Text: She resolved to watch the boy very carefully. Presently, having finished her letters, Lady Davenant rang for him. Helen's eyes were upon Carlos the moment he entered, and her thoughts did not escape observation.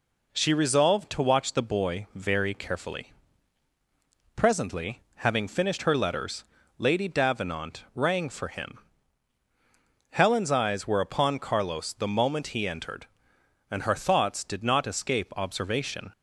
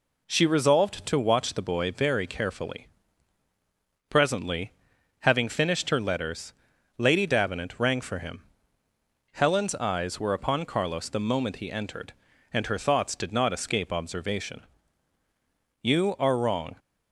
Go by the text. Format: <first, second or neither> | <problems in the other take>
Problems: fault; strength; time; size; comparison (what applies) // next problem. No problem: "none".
first | goes on to say "You are wrong"; noticeable; from 15.8 s on; 0.94 s long